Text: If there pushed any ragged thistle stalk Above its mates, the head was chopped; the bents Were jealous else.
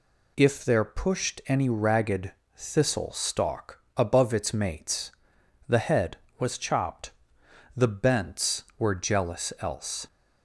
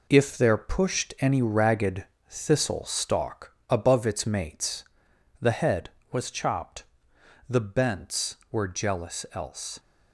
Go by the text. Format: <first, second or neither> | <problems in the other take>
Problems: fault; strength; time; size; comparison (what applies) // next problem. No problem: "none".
first | gets quieter; throughout; 7 dB // pauses between "ragged" and "thistle"; slight; at 2.0 s; 0.24 s long; slight in the first // pauses between "stalk" and "Above"; slight; at 3.5 s; 0.18 s long; slight in the first